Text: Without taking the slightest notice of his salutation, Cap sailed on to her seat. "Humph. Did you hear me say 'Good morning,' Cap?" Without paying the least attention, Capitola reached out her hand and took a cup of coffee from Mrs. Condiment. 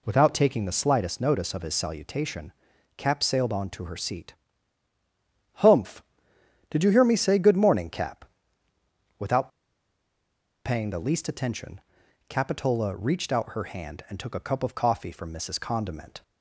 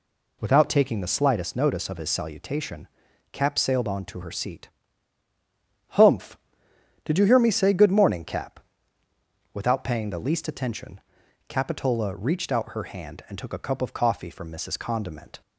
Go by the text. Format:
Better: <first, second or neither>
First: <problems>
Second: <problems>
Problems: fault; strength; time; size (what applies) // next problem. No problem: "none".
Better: second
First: pauses between "Without" and "paying"; at 9.4 s; 1.1 s long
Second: none